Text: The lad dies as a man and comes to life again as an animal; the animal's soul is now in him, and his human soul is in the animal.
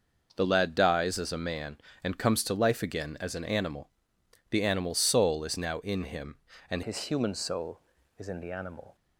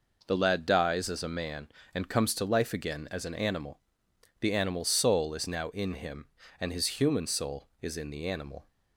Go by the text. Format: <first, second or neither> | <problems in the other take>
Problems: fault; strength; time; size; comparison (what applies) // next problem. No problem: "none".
second | changes voice at "his"; from 6.8 s on; 2.1 s long